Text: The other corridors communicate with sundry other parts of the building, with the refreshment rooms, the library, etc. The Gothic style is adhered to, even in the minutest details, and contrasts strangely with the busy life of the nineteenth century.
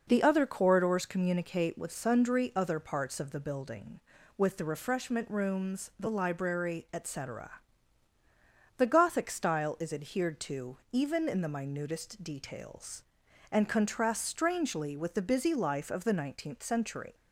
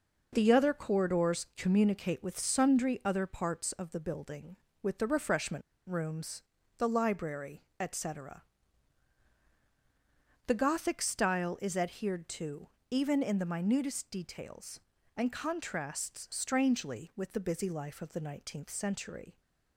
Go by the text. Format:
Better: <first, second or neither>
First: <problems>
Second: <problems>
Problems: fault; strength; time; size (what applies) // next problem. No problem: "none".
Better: first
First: none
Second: pauses between "refreshment" and "rooms"; slight; at 5.6 s; 0.27 s long